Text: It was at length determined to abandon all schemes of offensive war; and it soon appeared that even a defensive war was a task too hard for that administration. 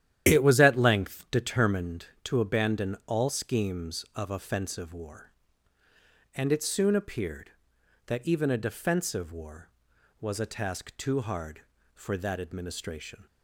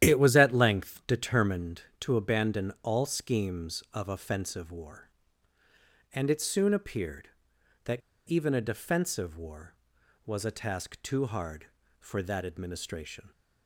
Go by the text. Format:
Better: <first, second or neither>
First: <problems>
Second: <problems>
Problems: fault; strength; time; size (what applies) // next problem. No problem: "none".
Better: first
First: starts louder than the rest; strong; until 1.3 s; 11 dB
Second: starts louder than the rest; strong; until 1.1 s; 11 dB // pauses between "that" and "even"; slight; at 8.0 s; 0.28 s long